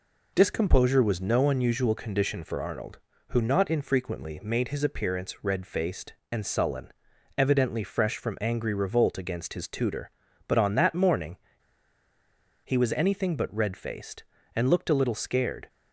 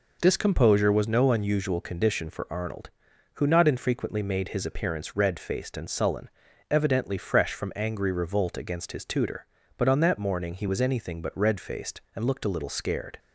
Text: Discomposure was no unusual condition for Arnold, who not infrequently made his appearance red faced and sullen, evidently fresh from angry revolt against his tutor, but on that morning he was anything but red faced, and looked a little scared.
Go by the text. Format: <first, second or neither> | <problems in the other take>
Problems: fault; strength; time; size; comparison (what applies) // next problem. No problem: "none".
second | pauses between "morning" and "he"; strong; at 11.3 s; 1.2 s long